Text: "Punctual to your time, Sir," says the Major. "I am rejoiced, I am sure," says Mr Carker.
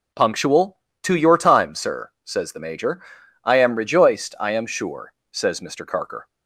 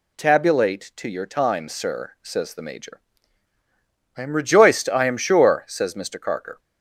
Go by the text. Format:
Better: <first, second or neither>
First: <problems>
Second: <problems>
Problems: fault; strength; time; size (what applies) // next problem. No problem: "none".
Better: first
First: none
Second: says "Tabulate" for "Punctual"; at 0.1 s